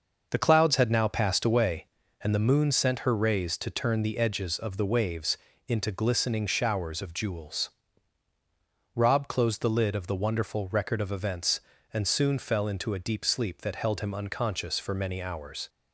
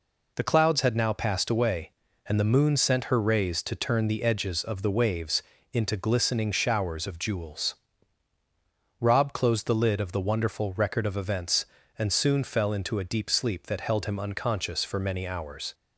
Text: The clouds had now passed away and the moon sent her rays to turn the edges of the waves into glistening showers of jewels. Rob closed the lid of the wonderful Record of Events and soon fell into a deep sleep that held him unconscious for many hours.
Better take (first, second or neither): second